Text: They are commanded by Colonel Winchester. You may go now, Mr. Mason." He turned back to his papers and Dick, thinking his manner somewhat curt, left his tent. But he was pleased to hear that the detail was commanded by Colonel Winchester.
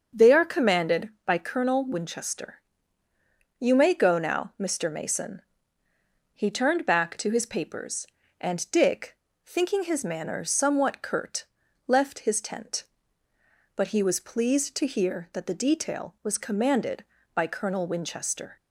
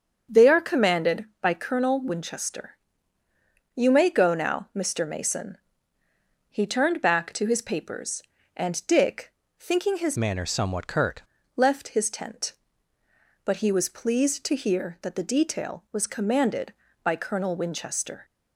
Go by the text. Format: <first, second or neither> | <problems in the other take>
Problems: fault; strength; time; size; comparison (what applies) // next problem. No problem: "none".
first | starts louder than the rest; until 1.4 s; 7 dB; also in the first // changes voice from "manner" to "curt"; from 10.1 to 11.2 s; 1.1 s long